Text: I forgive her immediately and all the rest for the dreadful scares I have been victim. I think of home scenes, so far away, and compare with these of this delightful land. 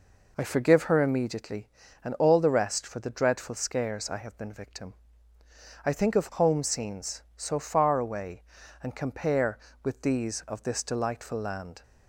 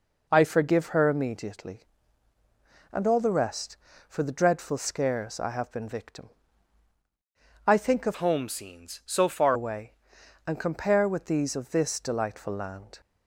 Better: first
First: none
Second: changes voice from "home" to "far"; from 8.1 to 9.5 s; 1.4 s long

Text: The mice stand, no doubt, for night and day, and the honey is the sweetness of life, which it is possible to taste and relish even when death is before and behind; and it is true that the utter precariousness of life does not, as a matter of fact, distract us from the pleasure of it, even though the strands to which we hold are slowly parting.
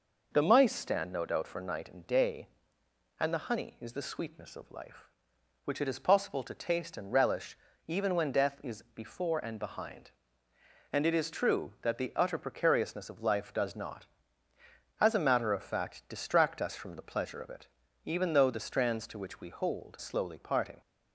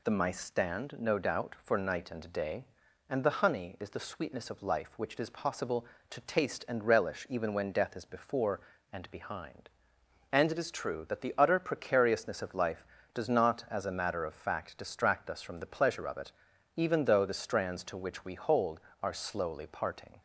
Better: second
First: pauses between "relish" and "even"; slight; at 7.5 s; 0.32 s long // skips "are"; at 19.9 s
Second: none

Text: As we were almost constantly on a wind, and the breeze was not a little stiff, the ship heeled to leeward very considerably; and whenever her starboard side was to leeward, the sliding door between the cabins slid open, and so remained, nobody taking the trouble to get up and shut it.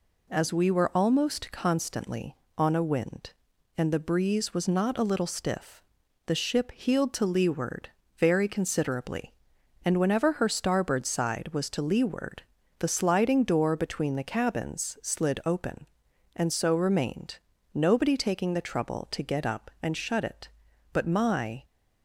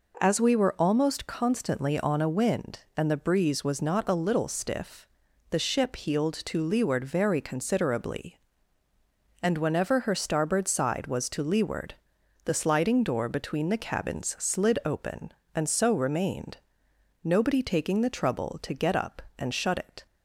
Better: second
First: pauses between "leeward" and "very"; slight; at 7.8 s; 0.30 s long // goes on to say "But my"; noticeable; from 20.9 s on; 0.72 s long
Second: none

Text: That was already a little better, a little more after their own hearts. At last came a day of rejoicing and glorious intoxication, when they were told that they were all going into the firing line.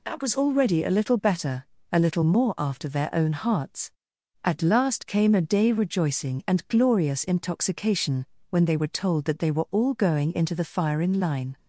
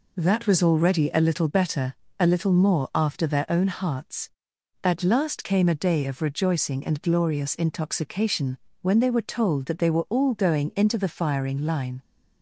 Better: second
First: skips "of"; at 5.7 s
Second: none

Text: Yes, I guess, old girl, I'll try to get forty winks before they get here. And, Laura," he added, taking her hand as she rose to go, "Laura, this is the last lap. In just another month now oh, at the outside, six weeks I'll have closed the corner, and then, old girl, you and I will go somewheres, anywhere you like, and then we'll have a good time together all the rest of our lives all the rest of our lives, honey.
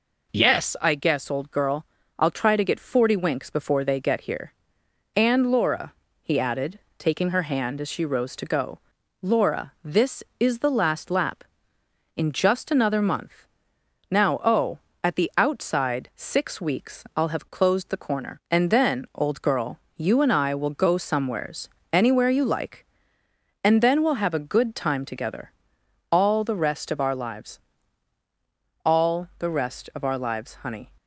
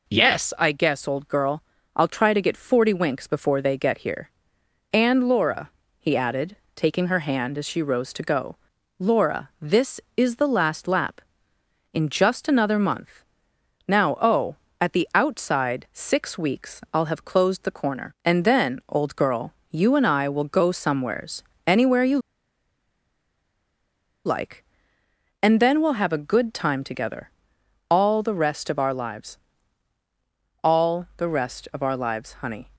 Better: first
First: pauses between "month" and "now"; noticeable; at 13.4 s; 0.64 s long // pauses between "together" and "all"; noticeable; at 25.5 s; 0.58 s long // pauses between "lives" and "all"; strong; at 27.5 s; 1.2 s long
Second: pauses between "month" and "now"; noticeable; at 13.2 s; 0.64 s long // pauses between "you" and "like"; strong; at 22.1 s; 2.0 s long // pauses between "together" and "all"; noticeable; at 27.3 s; 0.58 s long // pauses between "lives" and "all"; strong; at 29.3 s; 1.2 s long

